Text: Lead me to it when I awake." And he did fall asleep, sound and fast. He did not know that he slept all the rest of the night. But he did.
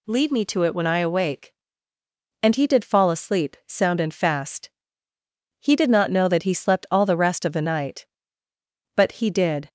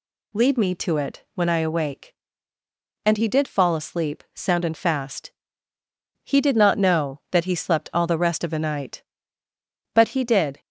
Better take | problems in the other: neither | none

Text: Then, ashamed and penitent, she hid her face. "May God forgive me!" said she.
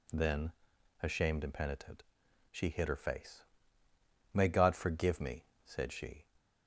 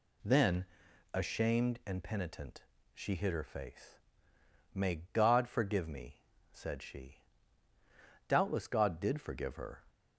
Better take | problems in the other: first | goes on to say "Doubtless God did forgive her"; from 8.2 s on; 1.5 s long

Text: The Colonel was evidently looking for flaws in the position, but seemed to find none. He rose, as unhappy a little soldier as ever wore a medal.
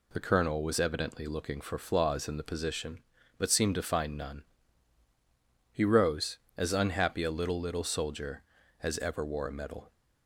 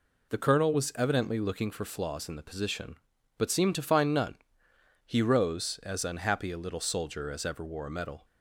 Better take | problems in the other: second | says "little" twice; at 7.6 s

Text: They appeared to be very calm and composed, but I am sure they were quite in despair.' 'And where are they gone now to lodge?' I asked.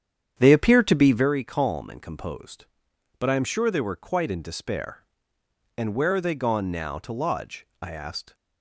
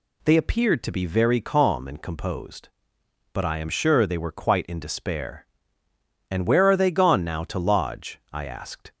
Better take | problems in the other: second | starts louder than the rest; strong; until 1.3 s; 8.5 dB

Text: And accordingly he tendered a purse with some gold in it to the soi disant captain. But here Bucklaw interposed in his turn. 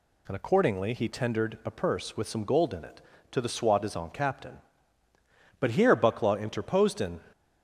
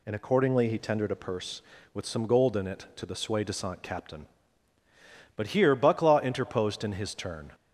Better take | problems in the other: second | stops before "his turn"; at 7.3 s

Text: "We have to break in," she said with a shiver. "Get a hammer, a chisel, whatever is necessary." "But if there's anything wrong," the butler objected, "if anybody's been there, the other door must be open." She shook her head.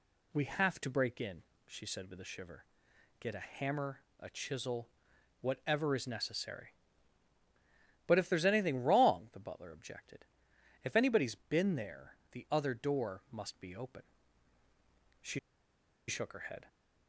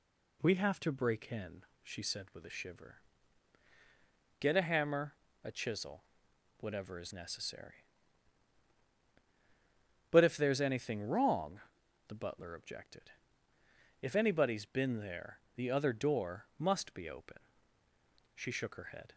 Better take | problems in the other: second | pauses between "She" and "shook"; noticeable; at 15.3 s; 0.68 s long

